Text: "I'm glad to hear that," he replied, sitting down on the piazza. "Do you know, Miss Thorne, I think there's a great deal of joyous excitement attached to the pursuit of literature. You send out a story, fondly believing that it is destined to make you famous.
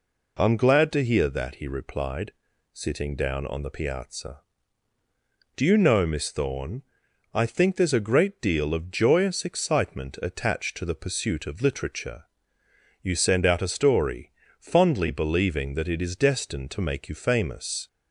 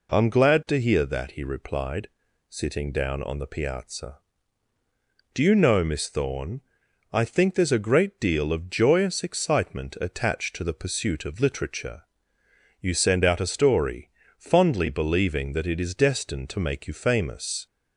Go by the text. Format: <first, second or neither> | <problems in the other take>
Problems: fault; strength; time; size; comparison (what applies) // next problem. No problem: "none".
neither | none